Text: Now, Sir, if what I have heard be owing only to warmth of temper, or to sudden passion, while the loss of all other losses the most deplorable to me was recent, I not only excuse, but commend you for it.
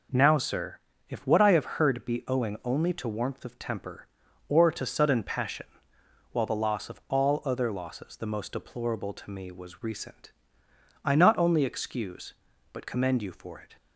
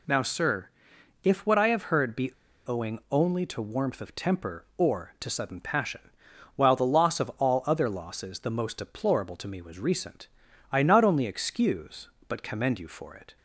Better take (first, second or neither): first